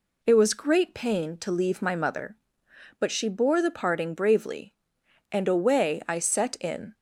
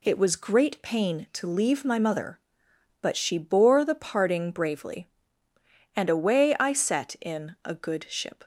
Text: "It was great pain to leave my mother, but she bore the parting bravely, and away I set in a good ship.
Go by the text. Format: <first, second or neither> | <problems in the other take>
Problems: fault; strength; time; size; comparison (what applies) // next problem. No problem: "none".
second | stops before "a good ship"; at 6.9 s